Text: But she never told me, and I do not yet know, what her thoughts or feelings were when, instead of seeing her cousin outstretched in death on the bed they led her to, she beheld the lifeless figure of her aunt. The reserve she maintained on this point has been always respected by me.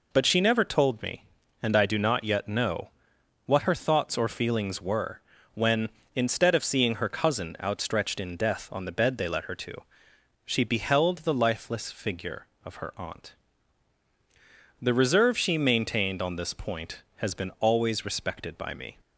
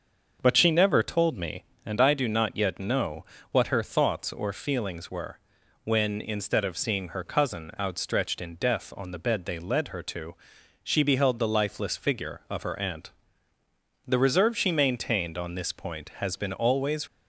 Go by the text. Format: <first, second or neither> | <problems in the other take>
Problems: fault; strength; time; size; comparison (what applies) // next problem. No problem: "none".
first | starts louder than the rest; until 1.4 s; 6.5 dB // pauses between "were" and "when"; noticeable; at 5.3 s; 0.46 s long; slight in the first // stops before "respected by me"; at 17.0 s